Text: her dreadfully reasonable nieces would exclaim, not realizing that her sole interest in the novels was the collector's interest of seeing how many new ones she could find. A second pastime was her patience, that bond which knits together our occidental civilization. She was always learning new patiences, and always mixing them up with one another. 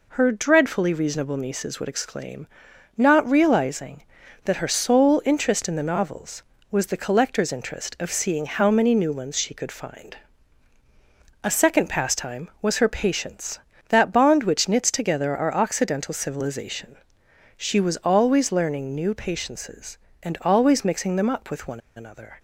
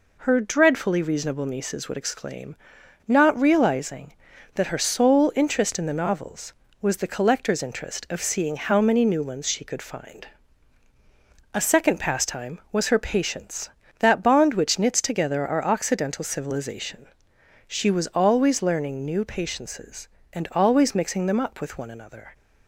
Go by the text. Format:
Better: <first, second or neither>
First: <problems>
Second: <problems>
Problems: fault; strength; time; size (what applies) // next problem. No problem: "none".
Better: second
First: pauses between "one" and "another"; slight; at 21.7 s; 0.16 s long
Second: none